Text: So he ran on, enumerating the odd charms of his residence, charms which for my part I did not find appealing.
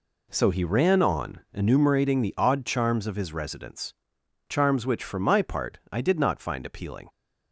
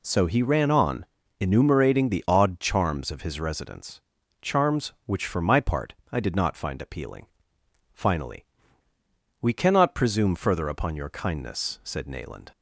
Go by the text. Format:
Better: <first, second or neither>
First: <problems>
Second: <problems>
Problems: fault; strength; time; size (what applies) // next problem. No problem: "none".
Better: first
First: none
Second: pauses between "part" and "I"; slight; at 5.9 s; 0.18 s long // goes on to say "Finally We cannot presume further upon your kindness said Nayland"; strong; from 7.9 s on; 4.5 s long